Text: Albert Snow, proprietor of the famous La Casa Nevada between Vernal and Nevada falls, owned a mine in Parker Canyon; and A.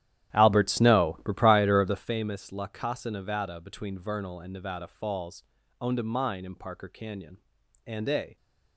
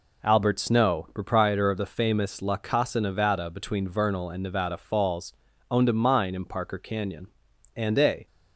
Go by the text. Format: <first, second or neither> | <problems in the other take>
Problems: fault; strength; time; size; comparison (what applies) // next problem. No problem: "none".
second | starts louder than the rest; strong; until 2.2 s; 12 dB